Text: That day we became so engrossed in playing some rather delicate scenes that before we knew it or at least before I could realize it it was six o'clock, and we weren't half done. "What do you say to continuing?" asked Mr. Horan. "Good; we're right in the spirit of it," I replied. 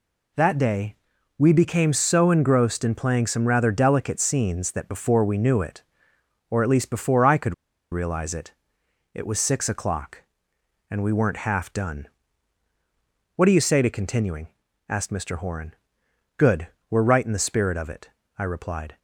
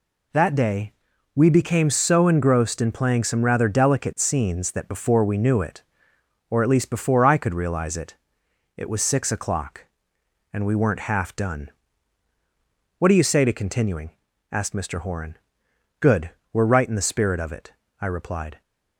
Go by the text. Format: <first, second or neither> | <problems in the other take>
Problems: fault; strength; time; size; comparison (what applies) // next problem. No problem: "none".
second | pauses between "day" and "we"; at 0.9 s; 0.42 s long; also in the second // pauses between "could" and "realize"; at 7.5 s; 0.37 s long // pauses between "it" and "it"; noticeable; at 8.5 s; 0.62 s long; noticeable in the second